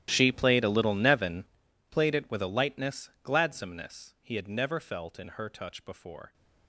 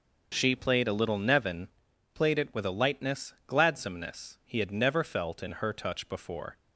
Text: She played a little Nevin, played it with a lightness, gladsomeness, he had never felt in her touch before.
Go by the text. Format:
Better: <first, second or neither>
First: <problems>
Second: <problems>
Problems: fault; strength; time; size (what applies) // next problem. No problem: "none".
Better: second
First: gets quieter; strong; throughout; 20.5 dB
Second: none